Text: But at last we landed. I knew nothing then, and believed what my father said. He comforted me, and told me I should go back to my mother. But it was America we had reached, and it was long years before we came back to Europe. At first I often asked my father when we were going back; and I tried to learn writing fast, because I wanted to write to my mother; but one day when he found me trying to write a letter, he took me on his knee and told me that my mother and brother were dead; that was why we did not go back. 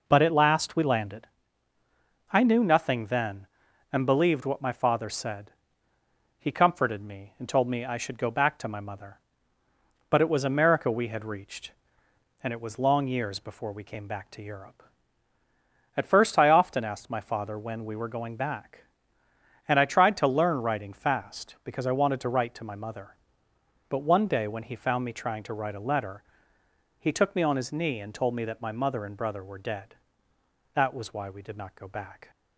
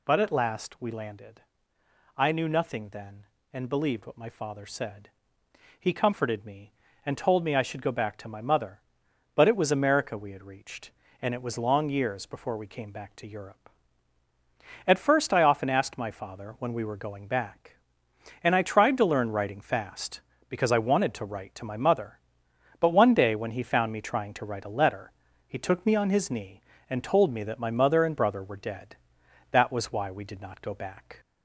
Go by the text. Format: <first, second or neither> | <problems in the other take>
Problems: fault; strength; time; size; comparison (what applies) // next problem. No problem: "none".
first | gets louder; slight; throughout; 2.5 dB